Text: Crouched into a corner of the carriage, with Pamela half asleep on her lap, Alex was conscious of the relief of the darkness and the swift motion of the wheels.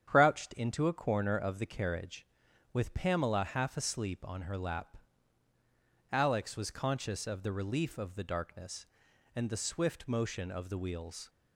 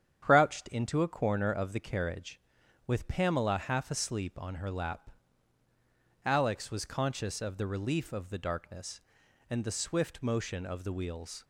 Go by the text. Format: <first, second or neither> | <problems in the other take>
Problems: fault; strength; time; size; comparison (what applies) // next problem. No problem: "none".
neither | starts louder than the rest; strong; the same in both